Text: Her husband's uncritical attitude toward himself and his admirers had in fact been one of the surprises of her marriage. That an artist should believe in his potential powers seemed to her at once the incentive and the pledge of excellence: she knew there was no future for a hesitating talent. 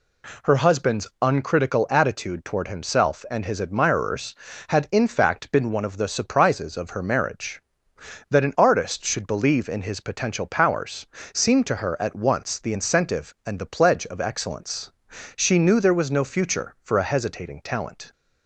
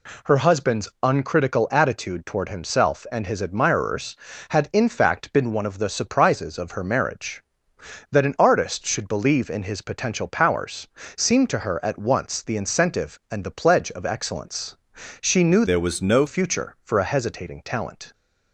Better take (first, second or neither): first